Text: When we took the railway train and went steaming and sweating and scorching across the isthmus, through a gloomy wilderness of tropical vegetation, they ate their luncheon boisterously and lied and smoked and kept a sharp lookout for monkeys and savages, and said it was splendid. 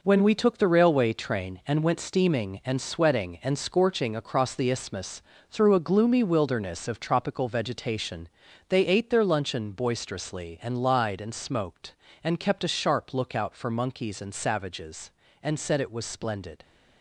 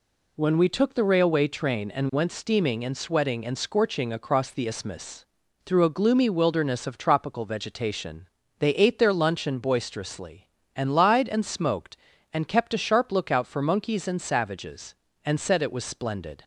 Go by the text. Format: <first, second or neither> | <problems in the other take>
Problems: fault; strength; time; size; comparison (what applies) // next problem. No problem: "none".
second | gets quieter; strong; throughout; 8 dB